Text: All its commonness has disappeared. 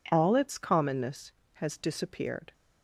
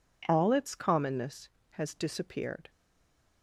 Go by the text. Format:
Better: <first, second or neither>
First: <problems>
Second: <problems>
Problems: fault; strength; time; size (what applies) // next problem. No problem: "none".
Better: first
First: none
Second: stays silent after the last word; slight; from 2.6 s on; 0.8 s long